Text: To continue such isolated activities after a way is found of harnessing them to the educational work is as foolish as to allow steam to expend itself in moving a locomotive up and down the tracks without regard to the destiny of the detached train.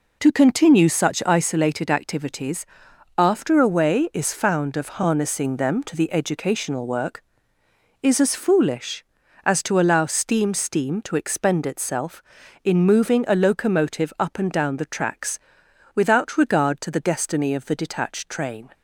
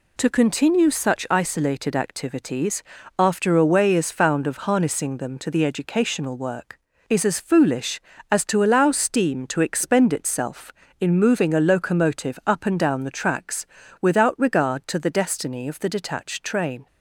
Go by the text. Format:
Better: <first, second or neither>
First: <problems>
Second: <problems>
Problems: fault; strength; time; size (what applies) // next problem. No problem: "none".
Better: second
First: pauses between "activities" and "after"; noticeable; at 2.6 s; 0.52 s long // says "steam" twice; at 10.5 s // pauses between "tracks" and "without"; noticeable; at 15.3 s; 0.58 s long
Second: pauses between "activities" and "after"; slight; at 2.8 s; 0.36 s long // pauses between "tracks" and "without"; slight; at 13.6 s; 0.34 s long